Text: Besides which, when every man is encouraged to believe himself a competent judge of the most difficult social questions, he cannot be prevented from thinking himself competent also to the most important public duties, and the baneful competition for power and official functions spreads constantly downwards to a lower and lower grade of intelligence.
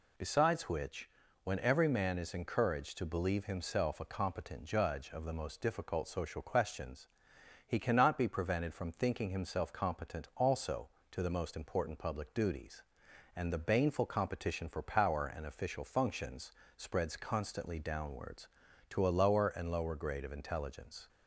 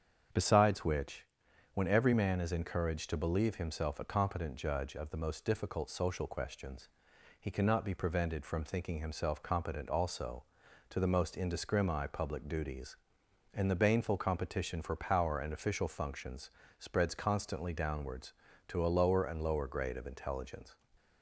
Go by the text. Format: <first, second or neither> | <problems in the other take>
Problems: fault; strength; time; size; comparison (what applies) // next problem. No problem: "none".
first | starts louder than the rest; strong; until 1.8 s; 7.5 dB // says "indiscrimi" for "important"; at 11.3 s // pauses between "functions" and "spreads"; slight; at 16.5 s; 0.28 s long; slight in the first